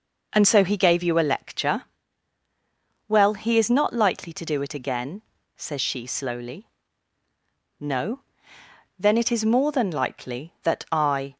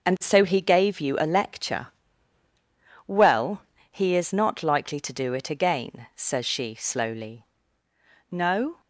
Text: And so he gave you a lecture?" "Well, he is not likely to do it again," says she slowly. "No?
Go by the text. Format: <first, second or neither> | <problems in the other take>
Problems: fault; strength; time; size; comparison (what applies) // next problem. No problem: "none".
second | goes on to say "Then it is more than likely that I"; strong; from 8.9 s on; 2.3 s long